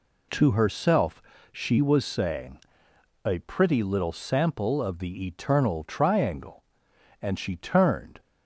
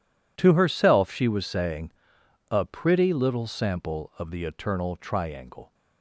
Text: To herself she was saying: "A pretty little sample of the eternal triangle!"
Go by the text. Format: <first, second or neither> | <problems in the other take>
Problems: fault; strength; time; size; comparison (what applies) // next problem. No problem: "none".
second | pauses between "herself" and "she"; slight; at 1.2 s; 0.28 s long // goes on to say "And she turned"; noticeable; from 7.1 s on; 1.0 s long